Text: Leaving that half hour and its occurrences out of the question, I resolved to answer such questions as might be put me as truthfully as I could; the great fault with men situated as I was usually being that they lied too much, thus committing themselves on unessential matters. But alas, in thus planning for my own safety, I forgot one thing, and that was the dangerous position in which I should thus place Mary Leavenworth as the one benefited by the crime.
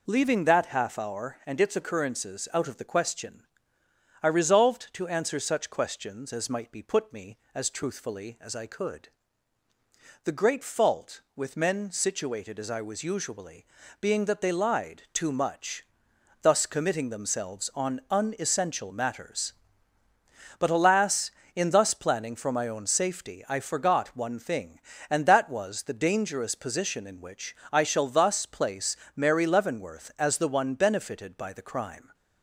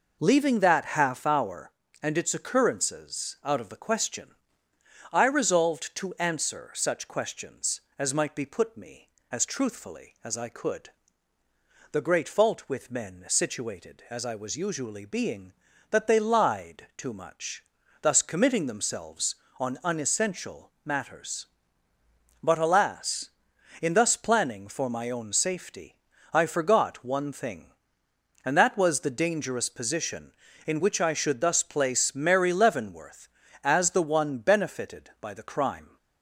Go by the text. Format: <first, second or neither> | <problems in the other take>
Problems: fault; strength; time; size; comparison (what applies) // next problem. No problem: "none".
second | pauses between "usually" and "being"; slight; at 13.6 s; 0.34 s long // pauses between "which" and "I"; slight; at 27.5 s; 0.16 s long // says "shall" for "should"; at 27.8 s // pauses between "place" and "Mary"; slight; at 28.9 s; 0.20 s long